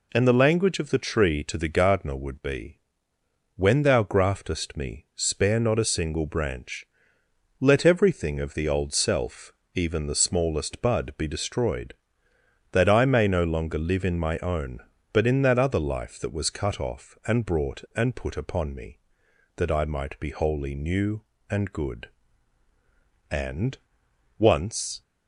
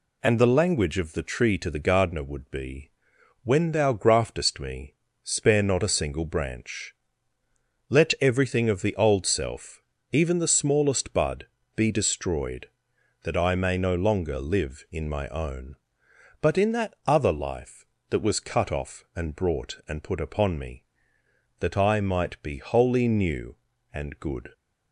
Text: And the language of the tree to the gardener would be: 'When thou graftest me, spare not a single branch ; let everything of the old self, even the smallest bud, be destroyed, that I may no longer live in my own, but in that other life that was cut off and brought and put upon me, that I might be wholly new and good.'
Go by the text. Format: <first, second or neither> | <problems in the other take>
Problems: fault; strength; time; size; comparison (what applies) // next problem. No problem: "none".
second | goes on to say "And once"; strong; from 23.2 s on; 1.7 s long